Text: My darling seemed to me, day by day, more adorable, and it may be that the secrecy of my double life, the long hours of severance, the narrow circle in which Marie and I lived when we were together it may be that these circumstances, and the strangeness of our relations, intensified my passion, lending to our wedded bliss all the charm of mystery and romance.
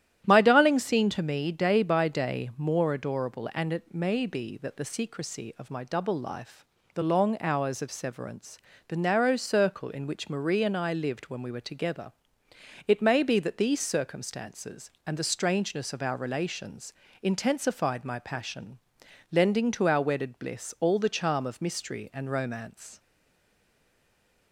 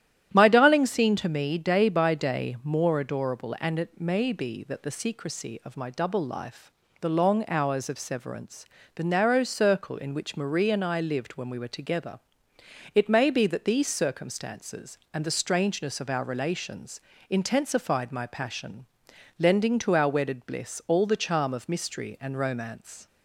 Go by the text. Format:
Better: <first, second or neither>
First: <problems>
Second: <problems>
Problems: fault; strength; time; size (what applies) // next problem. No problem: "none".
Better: second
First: starts louder than the rest; strong; until 1.2 s; 11.5 dB // pauses between "together" and "it"; noticeable; at 12.1 s; 0.76 s long // stays silent after the last word; noticeable; from 22.9 s on; 1.6 s long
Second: starts louder than the rest; strong; until 1.3 s; 11 dB // pauses between "together" and "it"; noticeable; at 12.1 s; 0.76 s long